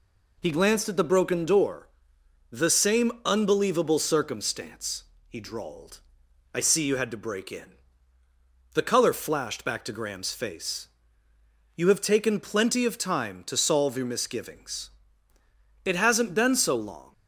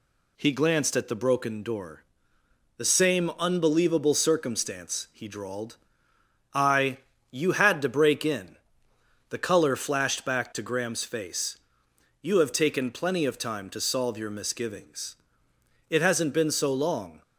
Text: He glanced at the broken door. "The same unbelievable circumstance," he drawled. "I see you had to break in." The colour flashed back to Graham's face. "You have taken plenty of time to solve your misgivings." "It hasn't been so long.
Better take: first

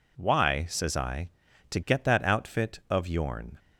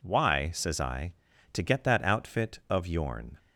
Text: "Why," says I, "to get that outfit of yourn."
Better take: neither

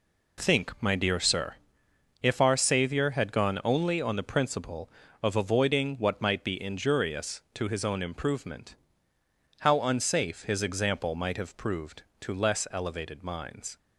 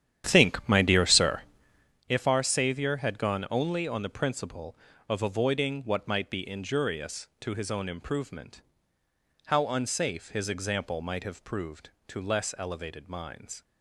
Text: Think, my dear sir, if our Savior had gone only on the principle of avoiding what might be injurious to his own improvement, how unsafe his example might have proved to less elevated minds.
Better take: first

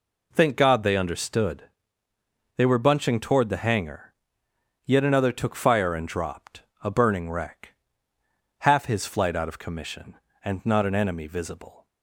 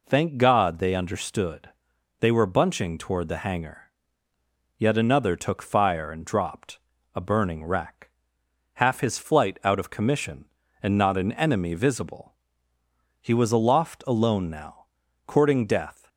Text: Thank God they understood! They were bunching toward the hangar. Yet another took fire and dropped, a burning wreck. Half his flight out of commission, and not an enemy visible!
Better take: first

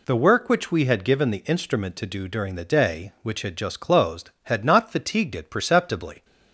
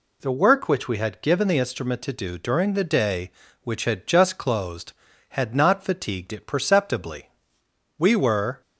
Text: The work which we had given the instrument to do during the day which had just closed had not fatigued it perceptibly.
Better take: first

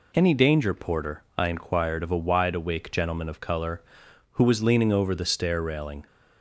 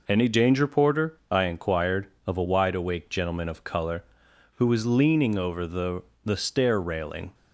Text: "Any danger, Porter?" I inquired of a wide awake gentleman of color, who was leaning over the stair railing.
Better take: first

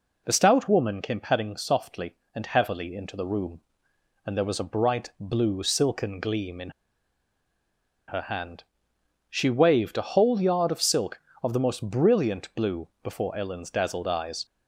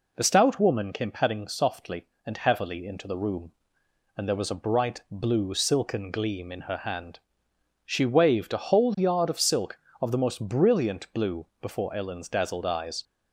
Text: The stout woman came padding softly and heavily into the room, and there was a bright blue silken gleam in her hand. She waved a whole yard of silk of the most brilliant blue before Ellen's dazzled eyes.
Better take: second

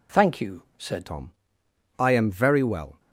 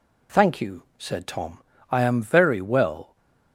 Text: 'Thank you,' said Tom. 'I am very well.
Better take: second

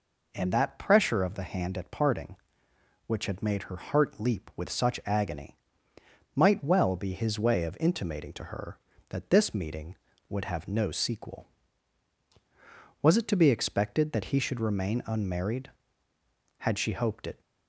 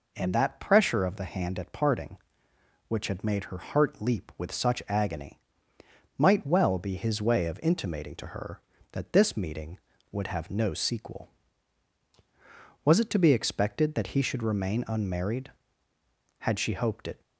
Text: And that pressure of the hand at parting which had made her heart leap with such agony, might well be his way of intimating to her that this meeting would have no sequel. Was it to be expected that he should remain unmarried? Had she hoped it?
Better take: neither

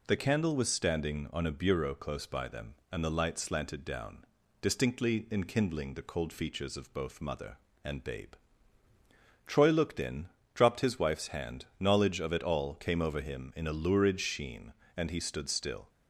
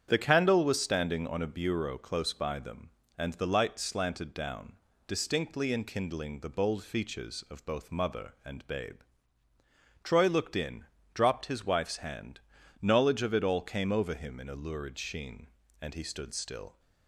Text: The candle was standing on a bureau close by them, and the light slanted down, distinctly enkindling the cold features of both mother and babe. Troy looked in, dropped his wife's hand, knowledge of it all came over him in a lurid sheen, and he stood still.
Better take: first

